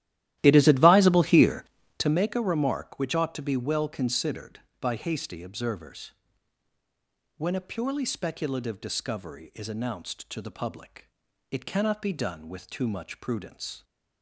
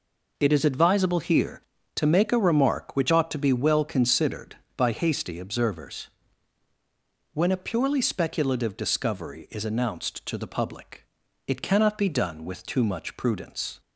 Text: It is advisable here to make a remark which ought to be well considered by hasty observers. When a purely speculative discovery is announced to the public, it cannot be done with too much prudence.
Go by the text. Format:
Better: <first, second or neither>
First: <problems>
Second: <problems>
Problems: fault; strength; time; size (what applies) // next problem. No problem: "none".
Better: second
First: starts louder than the rest; strong; until 2.2 s; 14 dB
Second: none